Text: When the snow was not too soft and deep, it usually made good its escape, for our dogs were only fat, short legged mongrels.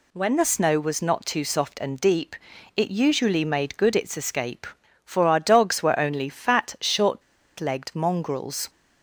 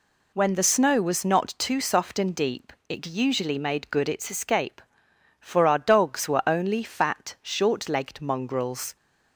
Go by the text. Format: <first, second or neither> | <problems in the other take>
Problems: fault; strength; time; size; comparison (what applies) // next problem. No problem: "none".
second | pauses between "short" and "legged"; at 7.2 s; 0.37 s long